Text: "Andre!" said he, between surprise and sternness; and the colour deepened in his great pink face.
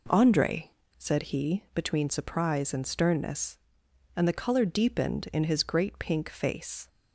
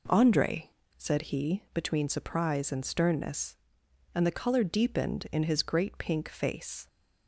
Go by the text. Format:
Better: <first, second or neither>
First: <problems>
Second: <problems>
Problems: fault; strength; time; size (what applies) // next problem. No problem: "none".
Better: neither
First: none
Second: none